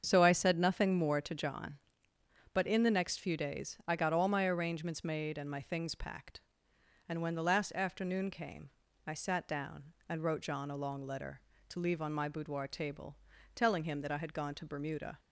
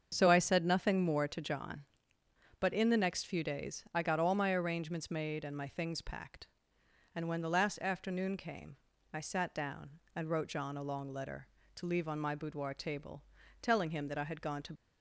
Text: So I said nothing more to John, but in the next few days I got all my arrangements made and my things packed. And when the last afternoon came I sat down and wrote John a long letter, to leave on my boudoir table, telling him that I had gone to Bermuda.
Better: first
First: starts louder than the rest; strong; until 1.0 s; 7.5 dB // pauses between "came" and "I"; at 8.6 s; 0.38 s long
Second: starts louder than the rest; until 1.1 s; 7 dB // pauses between "came" and "I"; at 8.7 s; 0.38 s long // stops before "Bermuda"; at 14.7 s

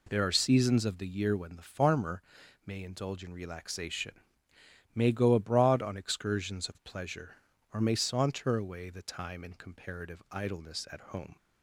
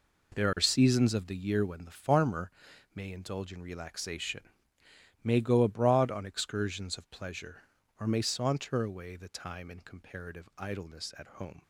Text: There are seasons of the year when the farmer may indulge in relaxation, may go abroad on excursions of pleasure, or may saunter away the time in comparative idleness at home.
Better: first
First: pauses between "farmer" and "may"; at 2.2 s; 0.44 s long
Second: gets quieter; strong; throughout; 11.5 dB // pauses between "farmer" and "may"; at 2.5 s; 0.44 s long

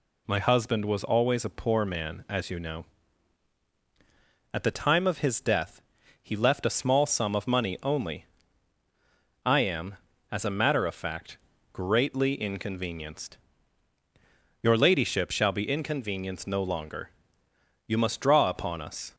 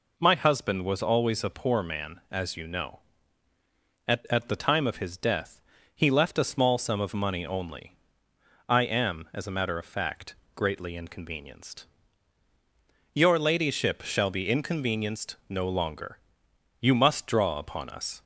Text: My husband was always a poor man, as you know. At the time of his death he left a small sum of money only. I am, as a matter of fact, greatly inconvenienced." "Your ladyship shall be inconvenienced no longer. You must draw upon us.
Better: first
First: pauses between "death" and "he"; at 5.8 s; 0.40 s long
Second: says "At" twice; at 4.3 s // pauses between "death" and "he"; slight; at 5.6 s; 0.34 s long // pauses between "inconvenienced" and "no"; slight; at 15.3 s; 0.16 s long

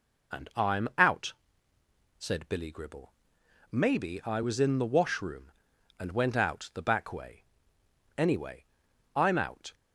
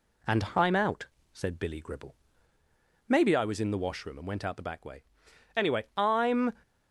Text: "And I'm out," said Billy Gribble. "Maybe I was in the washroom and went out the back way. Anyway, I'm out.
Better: first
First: none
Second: stops before "out"; at 6.6 s

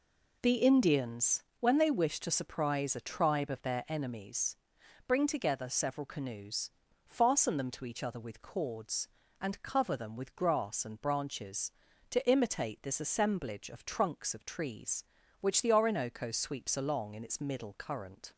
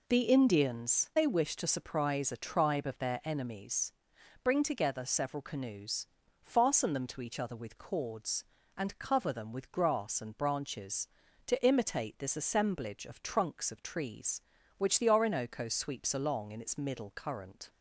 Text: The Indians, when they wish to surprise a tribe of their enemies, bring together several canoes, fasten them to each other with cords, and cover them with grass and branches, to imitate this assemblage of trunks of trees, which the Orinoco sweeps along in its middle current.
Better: first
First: none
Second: skips "when"; at 1.1 s

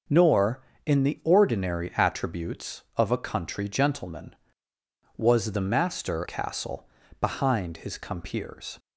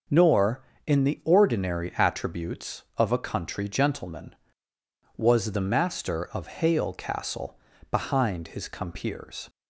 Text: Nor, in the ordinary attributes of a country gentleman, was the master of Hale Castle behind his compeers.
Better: second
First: starts louder than the rest; noticeable; until 1.4 s; 6 dB // skips "of Hale"; at 6.2 s // pauses between "Castle" and "behind"; slight; at 6.8 s; 0.34 s long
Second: pauses between "Castle" and "behind"; slight; at 7.5 s; 0.34 s long

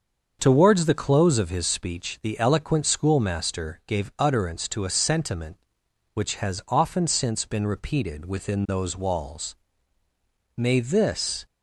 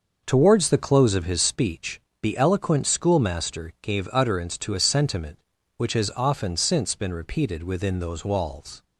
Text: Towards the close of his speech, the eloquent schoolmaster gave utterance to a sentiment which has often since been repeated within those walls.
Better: second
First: starts louder than the rest; until 1.4 s; 6.5 dB // goes on to say "May this"; noticeable; from 10.5 s on; 0.88 s long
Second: starts louder than the rest; noticeable; until 1.2 s; 6 dB

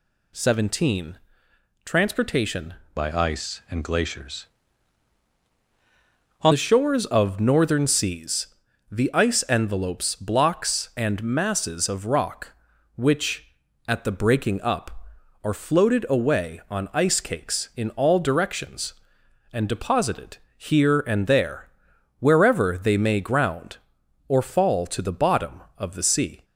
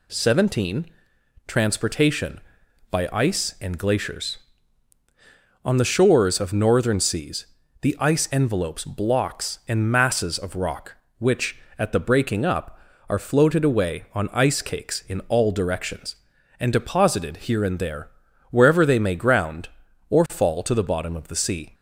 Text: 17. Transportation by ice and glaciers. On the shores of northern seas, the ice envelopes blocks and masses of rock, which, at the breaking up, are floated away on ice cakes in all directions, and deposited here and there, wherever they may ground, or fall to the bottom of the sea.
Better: second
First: changes voice from "by" to "On"; from 2.9 to 6.5 s; 3.6 s long // pauses between "deposited" and "here"; slight; at 20.3 s; 0.18 s long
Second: none

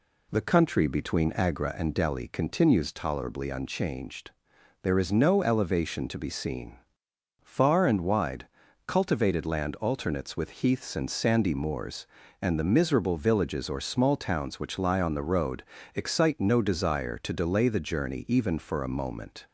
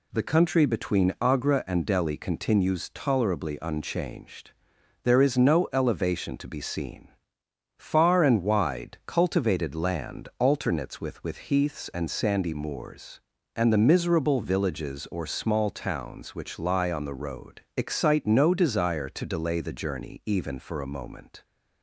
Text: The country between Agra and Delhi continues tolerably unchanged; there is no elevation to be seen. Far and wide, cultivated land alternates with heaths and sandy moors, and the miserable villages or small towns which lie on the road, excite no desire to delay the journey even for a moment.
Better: first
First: none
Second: says "with" twice; at 11.2 s

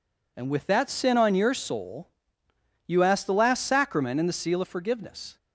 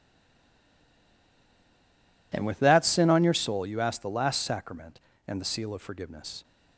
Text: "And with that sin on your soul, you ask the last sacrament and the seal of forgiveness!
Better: first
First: none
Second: stays silent before the first word; until 2.3 s; 2.3 s long

